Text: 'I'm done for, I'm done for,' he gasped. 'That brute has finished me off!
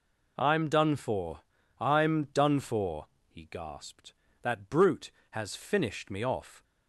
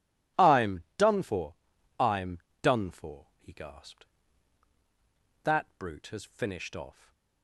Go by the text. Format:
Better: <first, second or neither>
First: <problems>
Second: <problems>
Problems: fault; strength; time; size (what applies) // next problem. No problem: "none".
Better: first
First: none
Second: pauses between "I'm" and "done"; slight; at 0.8 s; 0.16 s long // pauses between "I'm" and "done"; slight; at 2.3 s; 0.24 s long // skips "me"; at 6.7 s // stays silent after the last word; slight; from 6.9 s on; 0.5 s long